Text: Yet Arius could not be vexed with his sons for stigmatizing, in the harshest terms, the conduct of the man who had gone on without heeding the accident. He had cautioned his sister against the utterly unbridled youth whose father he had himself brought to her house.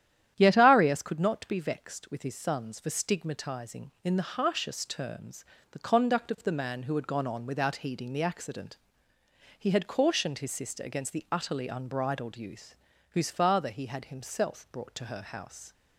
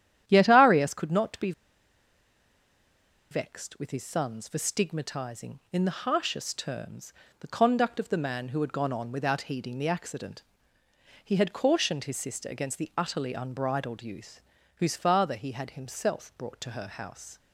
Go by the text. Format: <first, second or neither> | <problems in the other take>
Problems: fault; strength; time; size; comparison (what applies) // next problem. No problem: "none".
first | starts louder than the rest; strong; until 1.2 s; 11 dB; strong in the first // pauses between "be" and "vexed"; strong; at 1.5 s; 1.7 s long // pauses between "youth" and "whose"; slight; at 14.4 s; 0.36 s long; slight in the first